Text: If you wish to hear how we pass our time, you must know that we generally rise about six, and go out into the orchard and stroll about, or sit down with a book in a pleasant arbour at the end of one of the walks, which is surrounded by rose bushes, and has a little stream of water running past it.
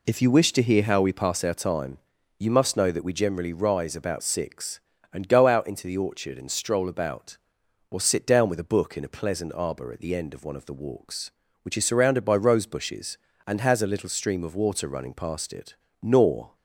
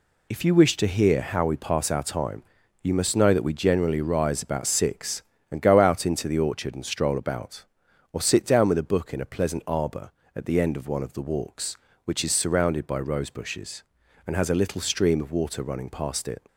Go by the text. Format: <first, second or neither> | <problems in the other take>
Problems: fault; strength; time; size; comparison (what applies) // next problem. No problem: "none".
second | goes on to say "Nor"; from 16.0 s on; 0.52 s long